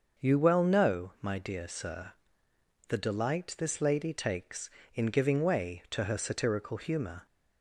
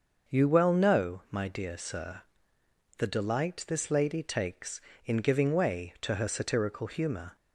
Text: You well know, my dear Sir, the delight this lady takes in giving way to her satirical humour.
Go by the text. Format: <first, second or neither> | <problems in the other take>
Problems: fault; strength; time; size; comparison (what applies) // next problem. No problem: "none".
neither | starts louder than the rest; the same in both